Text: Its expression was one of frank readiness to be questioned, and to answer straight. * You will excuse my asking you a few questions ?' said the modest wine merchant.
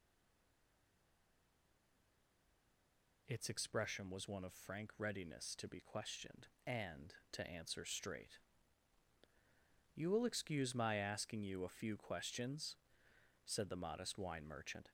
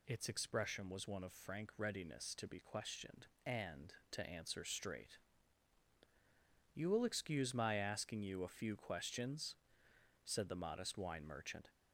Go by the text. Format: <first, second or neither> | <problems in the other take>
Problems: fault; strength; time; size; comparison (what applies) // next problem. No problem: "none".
second | stays silent before the first word; strong; until 3.2 s; 3.2 s long